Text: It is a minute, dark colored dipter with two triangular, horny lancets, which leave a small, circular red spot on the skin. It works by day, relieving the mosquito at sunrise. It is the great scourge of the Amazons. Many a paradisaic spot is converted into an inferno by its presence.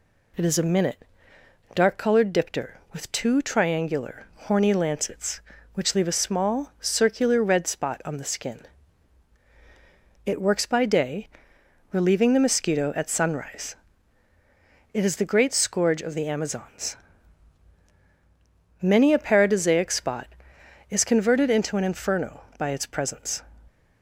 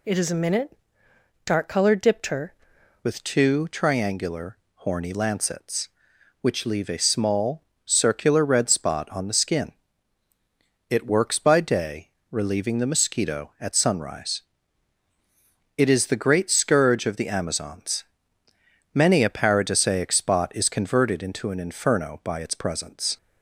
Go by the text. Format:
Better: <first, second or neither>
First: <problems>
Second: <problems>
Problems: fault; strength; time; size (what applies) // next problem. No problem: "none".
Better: first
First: none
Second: changes voice at "with"; from 3.0 s on; 20.1 s long